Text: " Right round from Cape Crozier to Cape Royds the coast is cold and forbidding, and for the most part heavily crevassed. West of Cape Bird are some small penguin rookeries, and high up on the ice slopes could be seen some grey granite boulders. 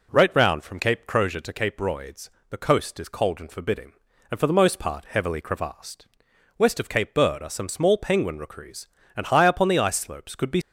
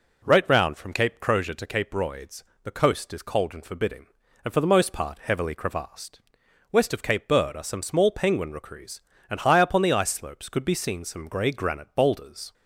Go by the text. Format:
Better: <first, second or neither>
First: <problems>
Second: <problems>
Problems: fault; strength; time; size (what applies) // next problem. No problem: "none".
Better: second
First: pauses between "Royds" and "the"; slight; at 2.2 s; 0.20 s long // stops before "seen some grey granite boulders"; at 10.6 s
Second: pauses between "Royds" and "the"; slight; at 2.4 s; 0.20 s long